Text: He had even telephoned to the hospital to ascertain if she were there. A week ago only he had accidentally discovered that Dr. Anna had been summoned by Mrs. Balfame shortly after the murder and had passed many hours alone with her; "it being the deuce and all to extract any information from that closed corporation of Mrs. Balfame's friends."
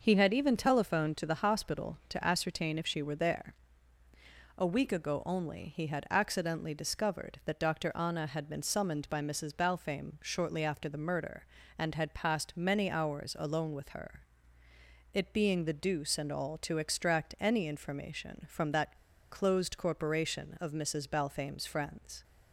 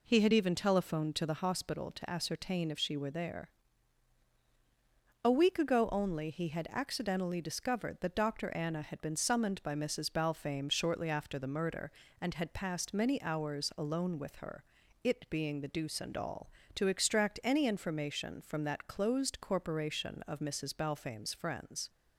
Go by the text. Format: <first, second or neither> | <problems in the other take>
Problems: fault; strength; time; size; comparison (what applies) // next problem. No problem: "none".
second | pauses between "that" and "closed"; slight; at 18.9 s; 0.34 s long